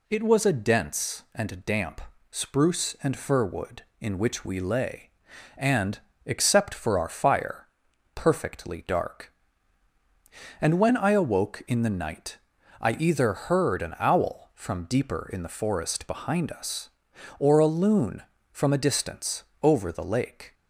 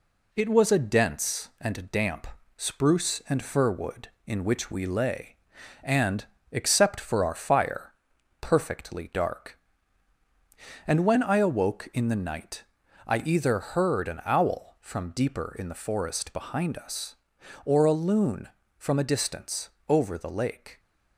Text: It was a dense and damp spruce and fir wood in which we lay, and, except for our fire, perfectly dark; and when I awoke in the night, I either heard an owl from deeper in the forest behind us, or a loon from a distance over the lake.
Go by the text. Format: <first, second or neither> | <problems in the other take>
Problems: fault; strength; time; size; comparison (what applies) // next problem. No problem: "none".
first | gets quieter; slight; throughout; 3 dB // pauses between "damp" and "spruce"; slight; at 2.2 s; 0.30 s long; slight in the first // pauses between "distance" and "over"; slight; at 19.6 s; 0.22 s long; slight in the first